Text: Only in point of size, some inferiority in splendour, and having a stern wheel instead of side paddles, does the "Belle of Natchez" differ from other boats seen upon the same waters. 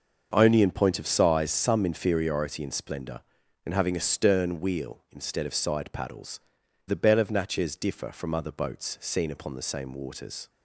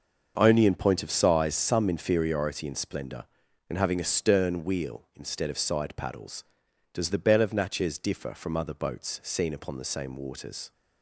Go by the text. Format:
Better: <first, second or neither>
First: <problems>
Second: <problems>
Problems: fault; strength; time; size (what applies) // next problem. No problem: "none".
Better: second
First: starts louder than the rest; until 1.3 s; 6.5 dB // skips "does"; at 6.6 s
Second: starts louder than the rest; until 1.3 s; 6.5 dB